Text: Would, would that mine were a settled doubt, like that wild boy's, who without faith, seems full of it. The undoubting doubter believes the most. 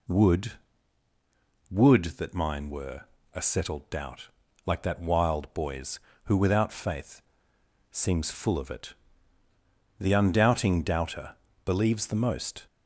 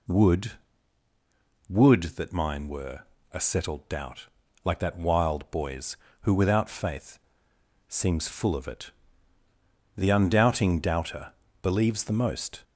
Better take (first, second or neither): neither